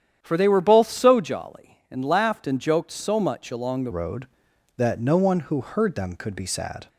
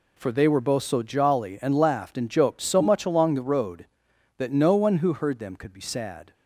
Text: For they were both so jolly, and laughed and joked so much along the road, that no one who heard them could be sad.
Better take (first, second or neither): second